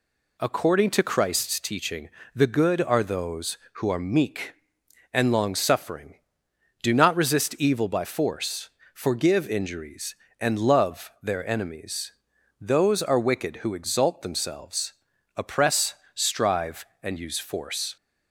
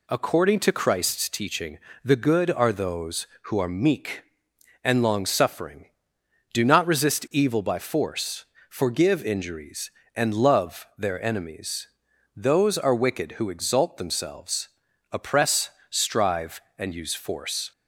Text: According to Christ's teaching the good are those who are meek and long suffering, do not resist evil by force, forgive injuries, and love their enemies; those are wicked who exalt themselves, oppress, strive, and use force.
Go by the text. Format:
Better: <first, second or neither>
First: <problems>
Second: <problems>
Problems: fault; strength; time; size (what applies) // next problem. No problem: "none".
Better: neither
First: pauses between "teaching" and "the"; slight; at 2.0 s; 0.26 s long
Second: pauses between "teaching" and "the"; slight; at 1.7 s; 0.26 s long